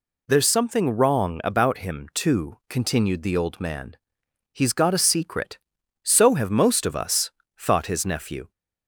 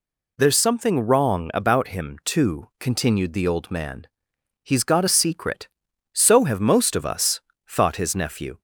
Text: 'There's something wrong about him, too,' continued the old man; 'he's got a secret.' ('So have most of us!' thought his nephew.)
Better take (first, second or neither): neither